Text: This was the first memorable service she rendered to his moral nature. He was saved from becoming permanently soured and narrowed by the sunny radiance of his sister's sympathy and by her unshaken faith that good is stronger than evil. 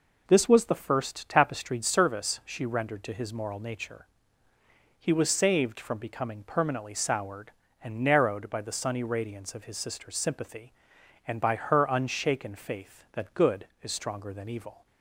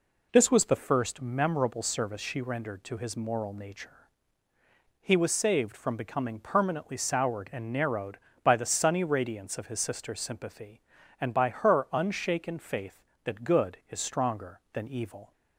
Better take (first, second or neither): second